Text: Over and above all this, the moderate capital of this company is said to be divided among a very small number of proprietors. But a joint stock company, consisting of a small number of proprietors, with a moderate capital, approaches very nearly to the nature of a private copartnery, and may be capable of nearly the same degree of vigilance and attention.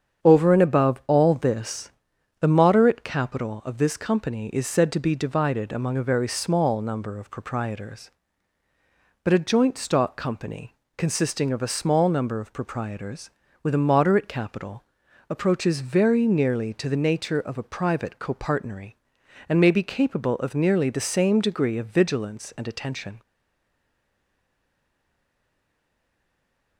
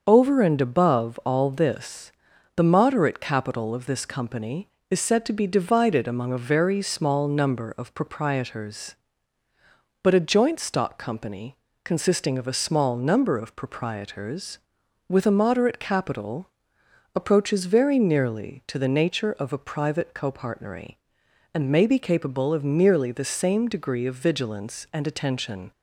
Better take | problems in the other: second | starts louder than the rest; strong; until 1.2 s; 8 dB; also in the second // stays silent after the last word; strong; from 23.2 s on; 3.5 s long

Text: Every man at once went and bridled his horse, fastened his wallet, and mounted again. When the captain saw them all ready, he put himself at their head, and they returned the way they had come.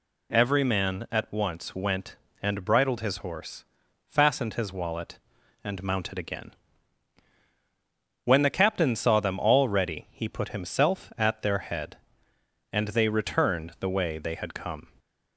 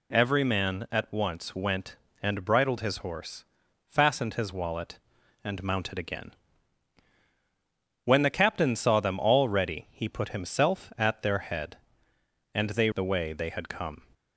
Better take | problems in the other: first | skips "returned"; at 12.9 s

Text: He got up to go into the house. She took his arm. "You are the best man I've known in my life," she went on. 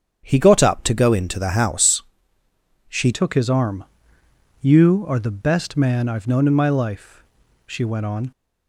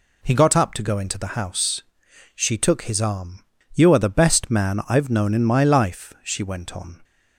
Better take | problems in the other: second | starts louder than the rest; strong; until 1.2 s; 8.5 dB // changes voice at "took"; from 3.1 s on; 5.2 s long

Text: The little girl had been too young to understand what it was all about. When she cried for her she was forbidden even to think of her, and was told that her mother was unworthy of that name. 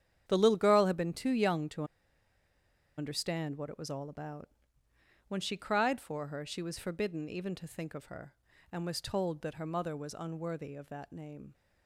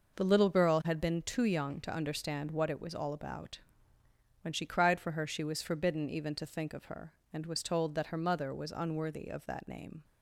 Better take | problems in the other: second | starts louder than the rest; strong; until 1.2 s; 9 dB // pauses between "to" and "understand"; at 1.8 s; 1.1 s long

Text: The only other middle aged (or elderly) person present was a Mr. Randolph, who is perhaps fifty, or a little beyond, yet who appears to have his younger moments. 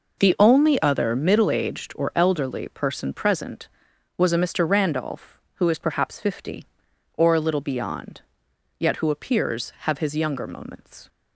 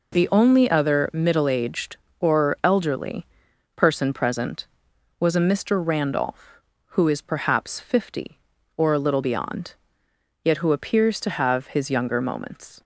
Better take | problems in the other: second | skips "to"; at 9.7 s

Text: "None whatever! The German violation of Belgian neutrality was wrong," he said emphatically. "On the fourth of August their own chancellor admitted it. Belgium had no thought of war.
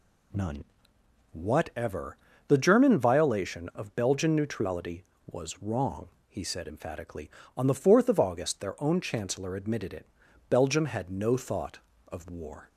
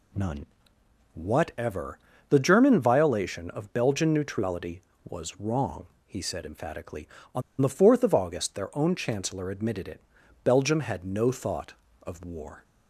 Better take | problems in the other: first | pauses between "None" and "whatever"; noticeable; at 0.4 s; 0.66 s long; noticeable in the first // pauses between "On" and "the"; slight; at 7.4 s; 0.19 s long

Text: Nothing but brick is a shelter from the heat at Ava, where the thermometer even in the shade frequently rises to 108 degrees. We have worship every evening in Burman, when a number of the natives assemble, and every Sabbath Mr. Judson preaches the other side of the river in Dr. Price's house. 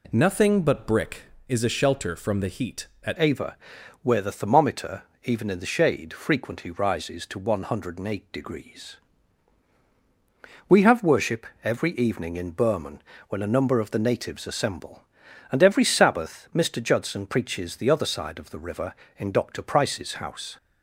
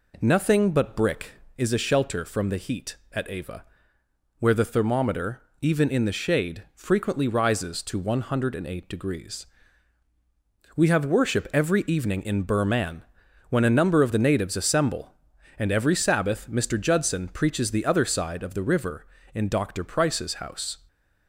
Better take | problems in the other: second | changes voice at "Ava"; from 3.1 s on; 17.4 s long // pauses between "thermometer" and "even"; slight; at 5.0 s; 0.22 s long; slight in the second // pauses between "worship" and "every"; slight; at 11.4 s; 0.18 s long

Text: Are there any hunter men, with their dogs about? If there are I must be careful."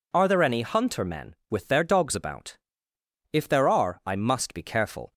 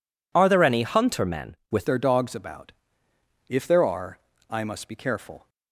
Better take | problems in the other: first | changes voice at "their"; from 1.8 s on; 3.6 s long // pauses between "are" and "I"; slight; at 4.1 s; 0.30 s long

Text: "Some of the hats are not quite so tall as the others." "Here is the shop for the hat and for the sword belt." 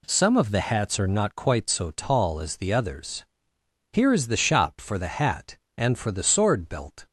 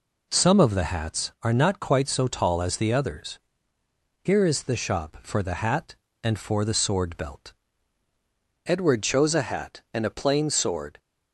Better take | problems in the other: first | goes on to say "Edward chose a hat and a plain sword"; strong; from 8.6 s on; 2.3 s long

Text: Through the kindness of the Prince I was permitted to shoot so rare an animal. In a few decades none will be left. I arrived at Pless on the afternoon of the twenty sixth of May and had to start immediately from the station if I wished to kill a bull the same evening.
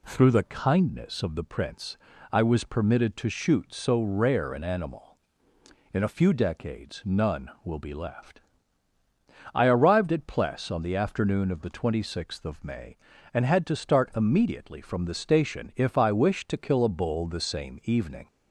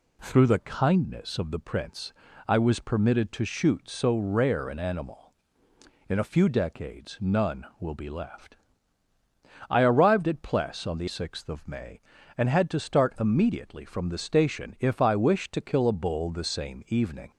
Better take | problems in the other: first | pauses between "Prince" and "I"; slight; at 2.1 s; 0.34 s long; slight in the first // skips "afternoon of the twenty"; at 11.0 s

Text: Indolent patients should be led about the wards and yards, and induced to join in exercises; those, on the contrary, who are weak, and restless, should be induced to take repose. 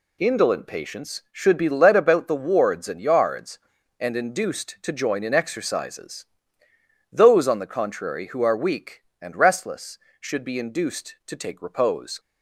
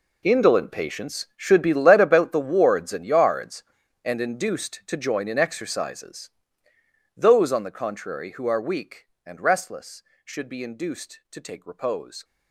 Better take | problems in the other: first | gets quieter; strong; throughout; 16 dB

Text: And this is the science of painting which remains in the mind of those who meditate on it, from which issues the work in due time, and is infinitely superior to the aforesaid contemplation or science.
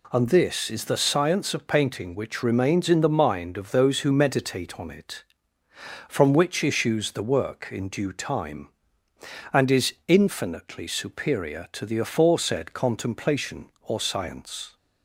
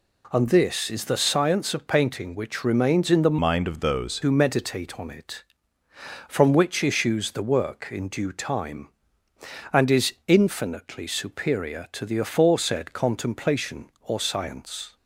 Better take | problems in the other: first | changes voice from "mind" to "those"; from 3.4 to 4.2 s; 0.8 s long

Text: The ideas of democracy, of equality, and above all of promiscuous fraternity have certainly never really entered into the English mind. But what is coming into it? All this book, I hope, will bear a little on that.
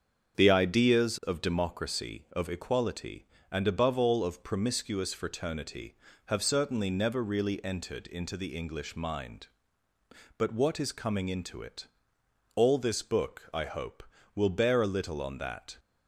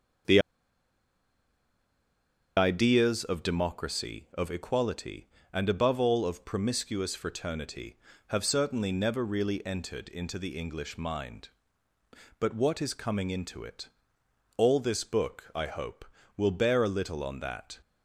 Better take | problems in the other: first | starts louder than the rest; until 3.4 s; 7 dB; also in the first // pauses between "The" and "ideas"; strong; at 0.3 s; 2.1 s long

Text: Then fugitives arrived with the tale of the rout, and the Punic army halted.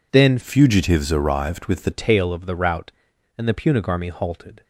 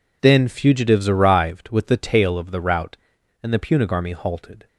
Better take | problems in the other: second | changes voice from "fugitives" to "the"; from 0.4 to 1.9 s; 1.5 s long

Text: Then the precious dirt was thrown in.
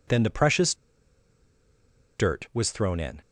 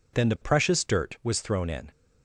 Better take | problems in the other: second | pauses between "precious" and "dirt"; strong; at 0.7 s; 1.4 s long

